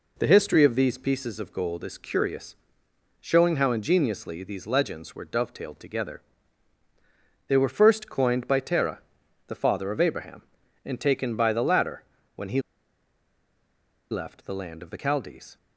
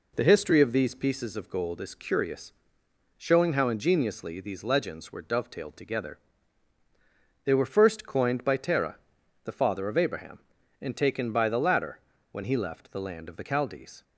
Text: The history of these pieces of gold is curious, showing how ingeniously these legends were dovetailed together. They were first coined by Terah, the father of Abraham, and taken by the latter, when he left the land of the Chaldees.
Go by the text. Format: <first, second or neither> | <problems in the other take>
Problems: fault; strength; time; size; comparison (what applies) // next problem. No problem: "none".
second | pauses between "he" and "left"; strong; at 12.6 s; 1.4 s long